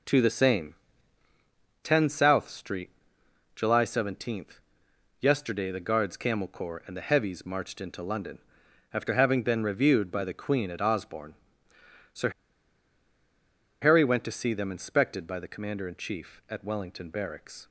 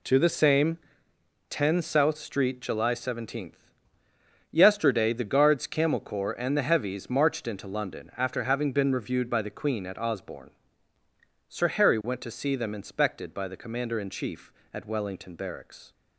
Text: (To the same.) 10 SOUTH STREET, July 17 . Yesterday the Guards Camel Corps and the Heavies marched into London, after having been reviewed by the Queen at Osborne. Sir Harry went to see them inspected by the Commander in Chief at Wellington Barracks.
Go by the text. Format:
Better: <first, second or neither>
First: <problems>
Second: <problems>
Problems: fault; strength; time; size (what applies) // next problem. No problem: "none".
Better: second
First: pauses between "Sir" and "Harry"; strong; at 12.3 s; 1.5 s long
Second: none